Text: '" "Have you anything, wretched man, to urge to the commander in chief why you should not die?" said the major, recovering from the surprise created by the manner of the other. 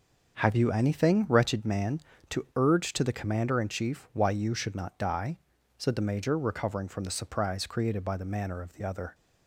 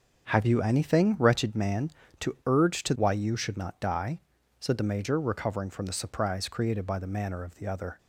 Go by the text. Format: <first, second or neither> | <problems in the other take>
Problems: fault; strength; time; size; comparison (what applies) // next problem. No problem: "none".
first | starts louder than the rest; strong; until 1.3 s; 7.5 dB; also in the first // skips "the commander in chief"; at 2.9 s